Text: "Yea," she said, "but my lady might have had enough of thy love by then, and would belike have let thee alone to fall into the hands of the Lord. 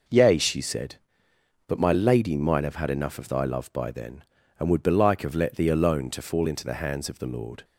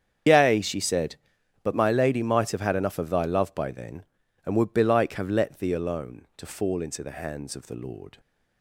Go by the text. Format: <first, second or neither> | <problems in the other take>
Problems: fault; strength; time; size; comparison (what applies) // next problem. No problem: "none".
first | loses the start of "Yea"; at 0.2 s; 60 ms // starts louder than the rest; strong; until 1.7 s; 8 dB